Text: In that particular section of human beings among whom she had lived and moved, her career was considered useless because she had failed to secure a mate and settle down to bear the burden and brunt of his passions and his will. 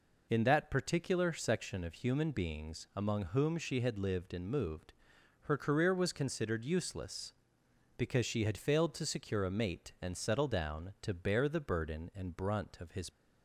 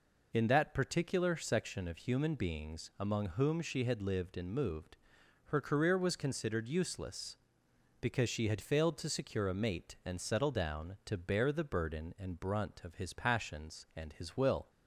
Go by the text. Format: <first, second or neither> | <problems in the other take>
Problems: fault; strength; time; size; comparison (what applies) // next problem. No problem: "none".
second | stops before "passions and his will"; at 13.0 s